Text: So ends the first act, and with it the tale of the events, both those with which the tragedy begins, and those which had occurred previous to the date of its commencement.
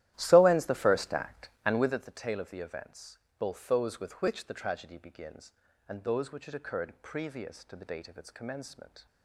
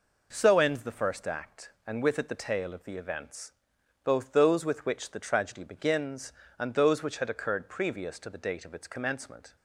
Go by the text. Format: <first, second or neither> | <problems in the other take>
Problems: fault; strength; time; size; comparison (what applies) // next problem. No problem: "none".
second | starts louder than the rest; strong; until 2.0 s; 13.5 dB